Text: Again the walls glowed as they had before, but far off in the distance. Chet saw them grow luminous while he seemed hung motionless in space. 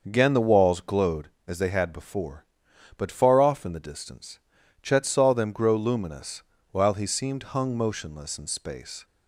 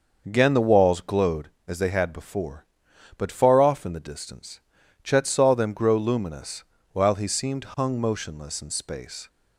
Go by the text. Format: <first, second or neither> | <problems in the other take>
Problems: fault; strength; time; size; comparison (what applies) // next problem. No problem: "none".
neither | pauses between "luminous" and "while"; slight; the same in both